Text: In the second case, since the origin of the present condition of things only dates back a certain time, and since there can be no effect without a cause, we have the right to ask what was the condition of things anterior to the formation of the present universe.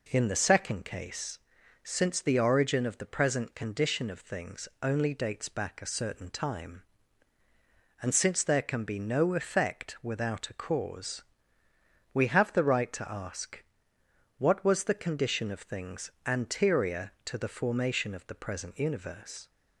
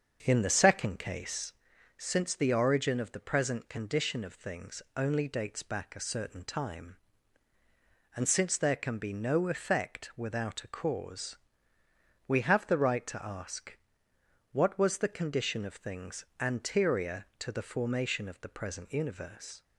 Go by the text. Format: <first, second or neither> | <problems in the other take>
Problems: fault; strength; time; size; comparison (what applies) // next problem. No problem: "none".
first | starts louder than the rest; until 1.7 s; 7 dB // pauses between "ask" and "what"; noticeable; at 13.7 s; 0.74 s long; noticeable in the first